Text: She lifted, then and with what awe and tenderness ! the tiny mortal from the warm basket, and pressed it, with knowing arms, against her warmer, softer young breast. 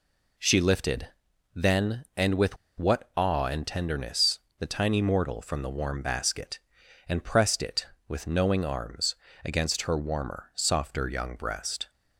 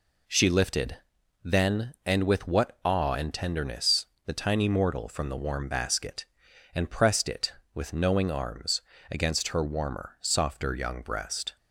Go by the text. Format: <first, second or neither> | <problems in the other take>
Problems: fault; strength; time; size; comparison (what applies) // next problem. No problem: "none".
second | pauses between "with" and "what"; slight; at 2.5 s; 0.22 s long